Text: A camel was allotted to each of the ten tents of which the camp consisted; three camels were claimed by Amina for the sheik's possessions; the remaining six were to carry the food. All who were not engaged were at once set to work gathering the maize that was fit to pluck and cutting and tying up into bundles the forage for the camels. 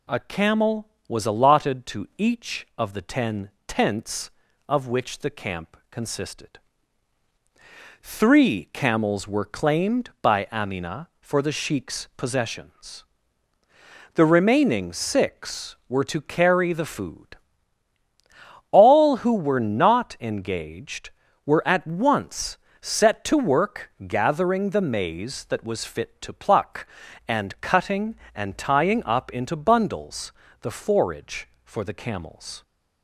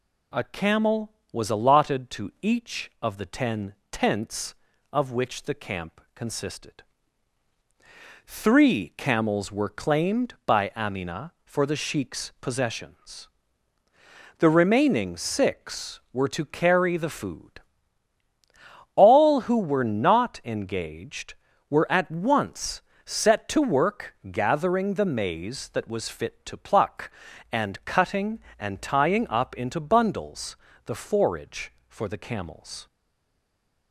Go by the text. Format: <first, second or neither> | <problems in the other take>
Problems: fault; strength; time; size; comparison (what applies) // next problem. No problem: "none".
first | pauses between "ten" and "tents"; slight; at 3.7 s; 0.16 s long; slight in the first // pauses between "once" and "set"; slight; at 22.8 s; 0.24 s long; slight in the first // pauses between "work" and "gathering"; slight; at 24.1 s; 0.16 s long; slight in the first // pauses between "bundles" and "the"; slight; at 30.5 s; 0.30 s long; slight in the first // stays silent after the last word; from 32.8 s on; 1.1 s long